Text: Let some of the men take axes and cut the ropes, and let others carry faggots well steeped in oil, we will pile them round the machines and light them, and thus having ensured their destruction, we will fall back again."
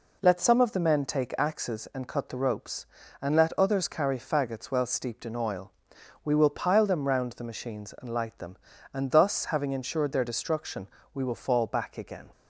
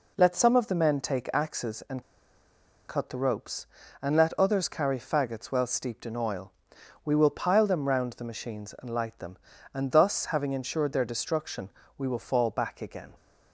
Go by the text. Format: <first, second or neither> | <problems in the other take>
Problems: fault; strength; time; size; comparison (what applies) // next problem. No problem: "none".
first | pauses between "and" and "cut"; noticeable; at 2.0 s; 0.85 s long